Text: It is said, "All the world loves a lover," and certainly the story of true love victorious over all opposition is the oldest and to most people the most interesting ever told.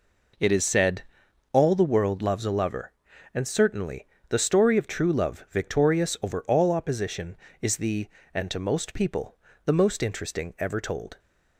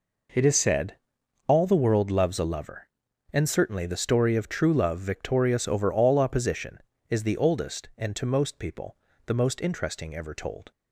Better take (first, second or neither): second